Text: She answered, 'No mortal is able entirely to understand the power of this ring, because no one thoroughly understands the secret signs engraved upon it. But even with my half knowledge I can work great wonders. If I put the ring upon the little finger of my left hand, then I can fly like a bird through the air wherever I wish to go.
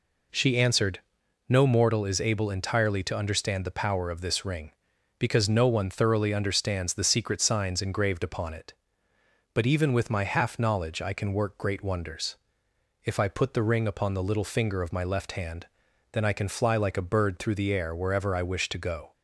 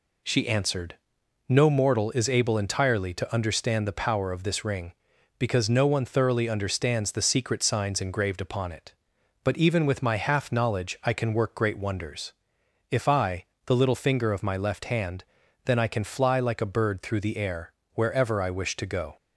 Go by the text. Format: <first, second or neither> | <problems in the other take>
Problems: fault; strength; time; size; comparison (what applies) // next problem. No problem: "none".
first | skips "put the ring upon"; at 13.5 s // pauses between "air" and "wherever"; slight; at 17.7 s; 0.22 s long